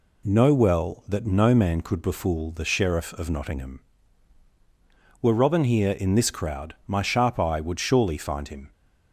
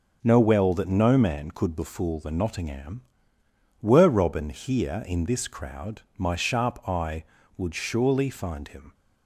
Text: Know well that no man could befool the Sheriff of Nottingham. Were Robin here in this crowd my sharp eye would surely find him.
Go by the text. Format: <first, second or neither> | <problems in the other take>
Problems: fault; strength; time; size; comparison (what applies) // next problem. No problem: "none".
first | skips "Sheriff of"; at 2.3 s // pauses between "crowd" and "my"; slight; at 6.0 s; 0.16 s long